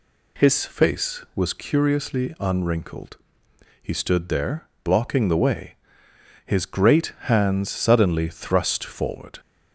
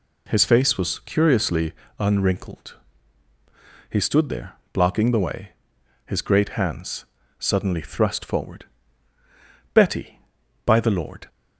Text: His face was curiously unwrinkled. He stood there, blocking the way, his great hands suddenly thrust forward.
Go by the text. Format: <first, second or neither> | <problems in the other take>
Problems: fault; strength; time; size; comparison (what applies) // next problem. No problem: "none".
first | pauses between "curiously" and "unwrinkled"; slight; at 1.7 s; 0.26 s long // pauses between "hands" and "suddenly"; slight; at 7.0 s; 0.34 s long // goes on to say "Betty by the Lord"; from 9.7 s on; 1.5 s long